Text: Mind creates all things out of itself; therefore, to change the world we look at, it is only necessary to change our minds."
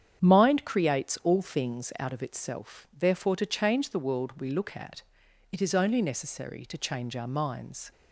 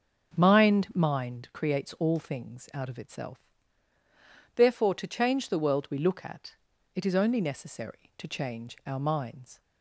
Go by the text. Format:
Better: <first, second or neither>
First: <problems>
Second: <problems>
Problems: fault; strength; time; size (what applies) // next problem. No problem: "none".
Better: first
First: starts louder than the rest; strong; until 1.2 s; 8.5 dB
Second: starts louder than the rest; strong; until 1.4 s; 7.5 dB // says "Mind" twice; at 0.9 s